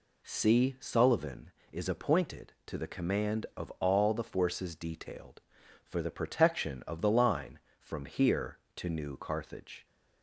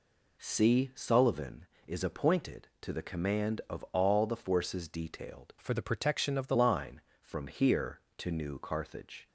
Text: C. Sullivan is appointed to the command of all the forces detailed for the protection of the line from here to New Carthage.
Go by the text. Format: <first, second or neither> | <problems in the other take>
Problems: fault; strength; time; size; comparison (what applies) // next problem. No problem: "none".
first | changes voice from "for" to "the"; from 5.5 to 6.5 s; 1.0 s long